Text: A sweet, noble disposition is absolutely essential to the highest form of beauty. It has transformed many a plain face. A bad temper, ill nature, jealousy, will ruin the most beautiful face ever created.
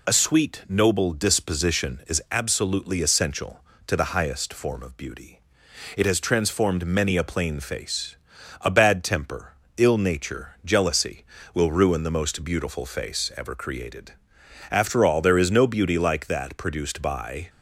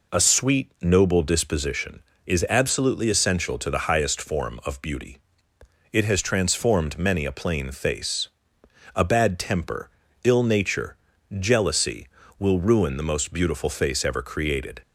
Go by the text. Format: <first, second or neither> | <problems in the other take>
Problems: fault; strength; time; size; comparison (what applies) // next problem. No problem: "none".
second | goes on to say "After all there is no beauty like that produced by"; strong; from 14.7 s on; 2.7 s long